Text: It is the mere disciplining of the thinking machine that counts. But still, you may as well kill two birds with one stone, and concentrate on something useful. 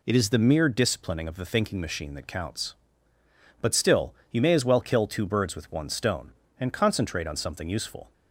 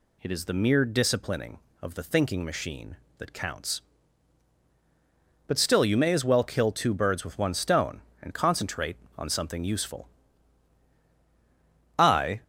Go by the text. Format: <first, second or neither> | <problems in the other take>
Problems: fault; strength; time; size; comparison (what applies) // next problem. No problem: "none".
first | goes on to say "I"; slight; from 11.9 s on; 0.44 s long